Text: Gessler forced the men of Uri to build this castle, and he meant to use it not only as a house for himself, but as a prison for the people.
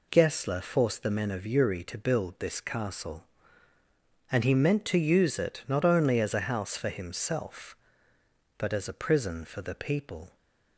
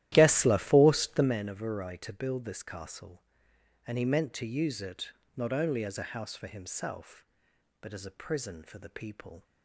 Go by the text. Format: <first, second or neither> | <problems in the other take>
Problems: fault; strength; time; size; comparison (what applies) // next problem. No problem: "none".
first | starts louder than the rest; strong; until 1.3 s; 13.5 dB // pauses between "it" and "not"; slight; at 5.1 s; 0.24 s long